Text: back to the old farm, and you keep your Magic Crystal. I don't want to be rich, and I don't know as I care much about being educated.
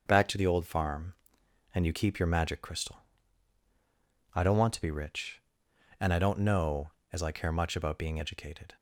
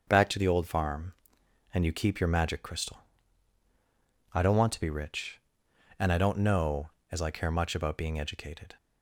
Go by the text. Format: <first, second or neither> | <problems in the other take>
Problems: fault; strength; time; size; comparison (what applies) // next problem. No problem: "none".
neither | starts louder than the rest; the same in both